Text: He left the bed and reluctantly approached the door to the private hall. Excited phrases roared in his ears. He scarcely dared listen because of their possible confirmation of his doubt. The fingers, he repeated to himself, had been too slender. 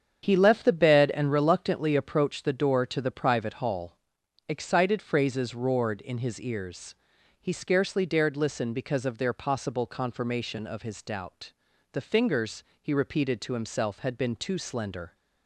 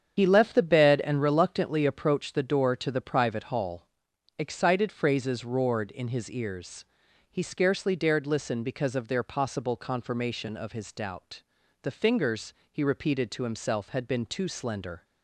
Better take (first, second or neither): first